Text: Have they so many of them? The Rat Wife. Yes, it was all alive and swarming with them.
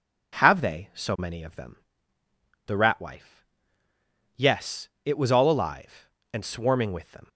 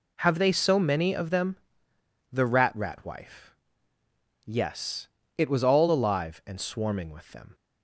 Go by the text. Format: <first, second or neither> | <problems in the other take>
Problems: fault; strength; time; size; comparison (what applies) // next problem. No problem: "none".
first | says "Rat" twice; at 2.7 s